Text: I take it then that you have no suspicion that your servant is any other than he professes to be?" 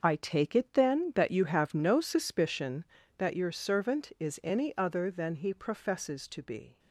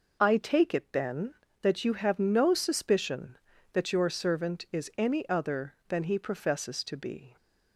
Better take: second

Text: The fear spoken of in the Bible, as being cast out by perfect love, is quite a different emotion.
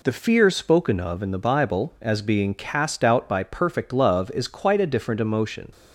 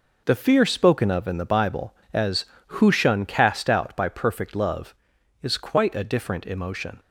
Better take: first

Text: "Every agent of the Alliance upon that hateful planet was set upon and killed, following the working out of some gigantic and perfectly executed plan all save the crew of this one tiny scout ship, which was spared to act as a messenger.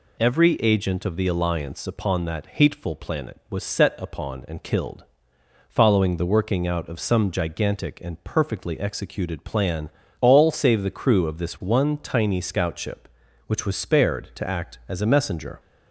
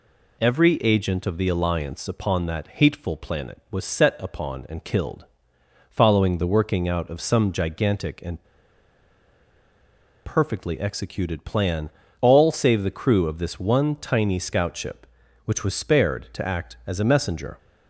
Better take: first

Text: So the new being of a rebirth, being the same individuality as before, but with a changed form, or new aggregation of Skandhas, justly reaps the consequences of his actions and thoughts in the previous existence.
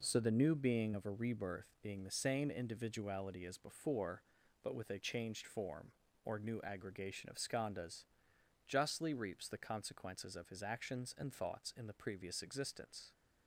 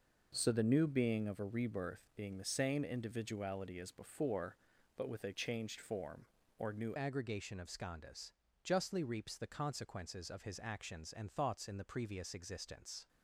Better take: first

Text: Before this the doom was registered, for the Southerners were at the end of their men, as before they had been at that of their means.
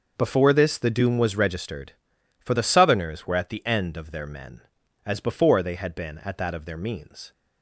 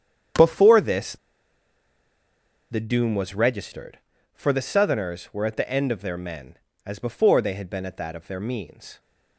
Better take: first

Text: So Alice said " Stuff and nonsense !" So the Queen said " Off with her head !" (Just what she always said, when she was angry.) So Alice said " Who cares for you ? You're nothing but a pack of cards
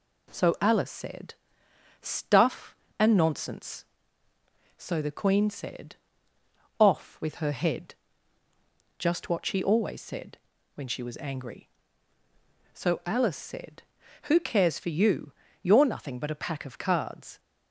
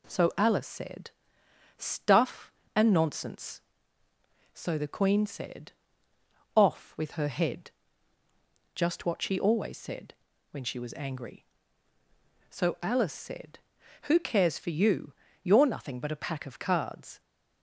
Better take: neither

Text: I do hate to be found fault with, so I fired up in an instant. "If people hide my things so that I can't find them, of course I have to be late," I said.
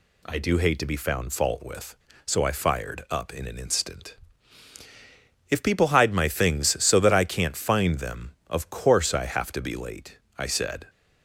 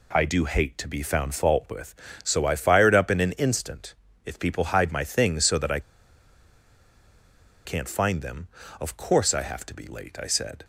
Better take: first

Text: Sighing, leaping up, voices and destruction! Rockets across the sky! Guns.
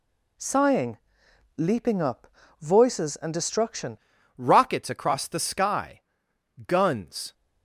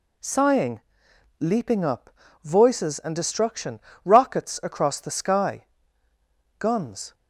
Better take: second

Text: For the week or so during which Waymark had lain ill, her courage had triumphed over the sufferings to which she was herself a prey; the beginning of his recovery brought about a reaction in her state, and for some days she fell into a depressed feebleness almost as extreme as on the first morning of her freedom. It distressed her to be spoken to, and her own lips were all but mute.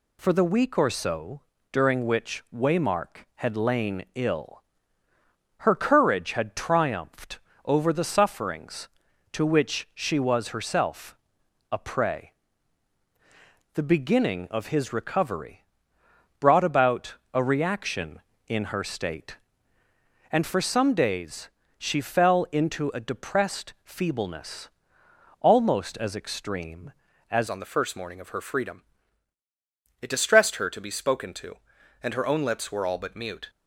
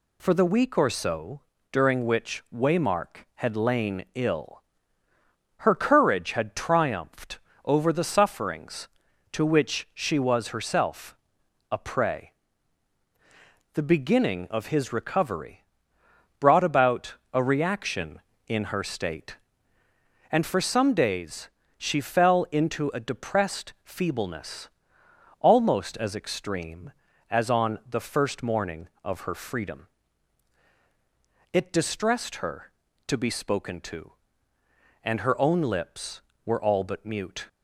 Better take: second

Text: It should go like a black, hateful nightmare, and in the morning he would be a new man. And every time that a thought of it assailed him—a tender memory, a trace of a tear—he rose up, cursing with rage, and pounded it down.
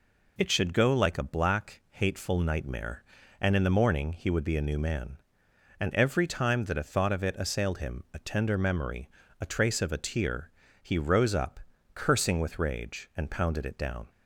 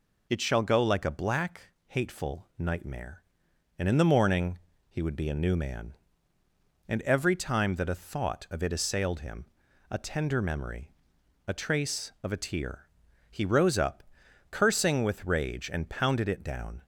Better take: first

